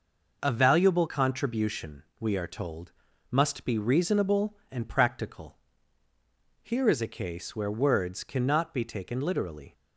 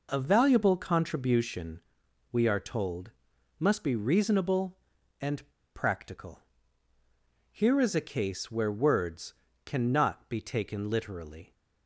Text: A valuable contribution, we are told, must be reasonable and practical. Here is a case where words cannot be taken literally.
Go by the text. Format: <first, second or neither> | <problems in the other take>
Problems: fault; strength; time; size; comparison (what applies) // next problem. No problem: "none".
first | pauses between "and" and "practical"; slight; at 5.4 s; 0.27 s long // pauses between "words" and "cannot"; slight; at 9.3 s; 0.28 s long